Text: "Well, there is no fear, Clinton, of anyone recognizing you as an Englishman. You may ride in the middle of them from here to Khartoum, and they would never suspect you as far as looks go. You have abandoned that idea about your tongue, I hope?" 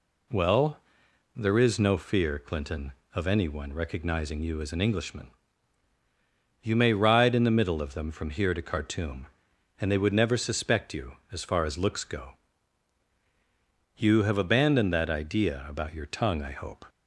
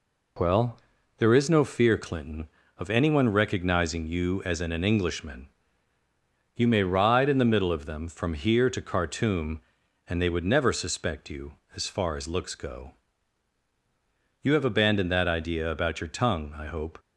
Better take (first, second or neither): first